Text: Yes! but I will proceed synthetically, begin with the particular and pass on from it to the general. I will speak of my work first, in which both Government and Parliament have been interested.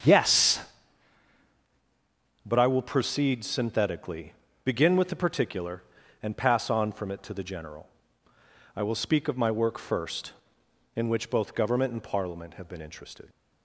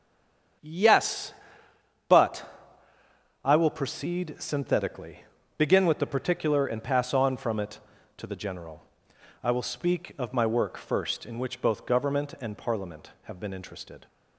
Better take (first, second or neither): first